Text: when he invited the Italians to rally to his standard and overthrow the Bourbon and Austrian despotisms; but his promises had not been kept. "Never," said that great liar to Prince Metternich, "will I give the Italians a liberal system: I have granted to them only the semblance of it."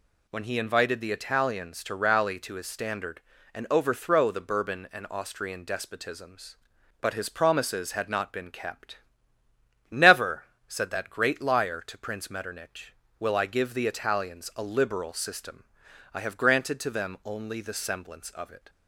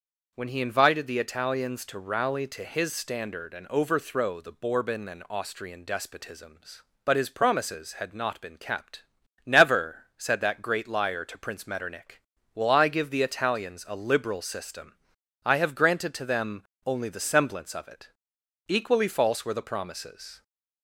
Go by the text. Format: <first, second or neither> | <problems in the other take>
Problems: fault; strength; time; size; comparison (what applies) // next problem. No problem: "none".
first | starts louder than the rest; noticeable; until 1.3 s; 6 dB // pauses between "them" and "only"; slight; at 16.6 s; 0.24 s long // goes on to say "Equally false were the promises"; strong; from 18.6 s on; 1.7 s long